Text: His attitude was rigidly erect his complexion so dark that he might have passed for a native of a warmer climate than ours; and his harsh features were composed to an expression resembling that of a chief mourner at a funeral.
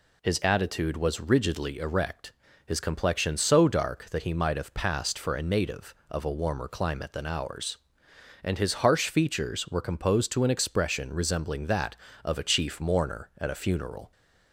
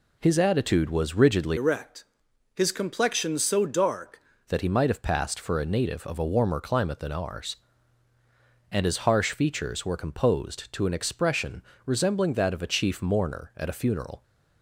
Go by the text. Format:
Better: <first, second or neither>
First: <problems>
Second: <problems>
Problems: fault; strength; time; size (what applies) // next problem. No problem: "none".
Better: first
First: pauses between "erect" and "his"; slight; at 2.3 s; 0.32 s long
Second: changes voice from "erect" to "dark"; from 1.5 to 4.1 s; 2.6 s long // pauses between "erect" and "his"; noticeable; at 2.0 s; 0.52 s long // pauses between "expression" and "resembling"; slight; at 11.6 s; 0.24 s long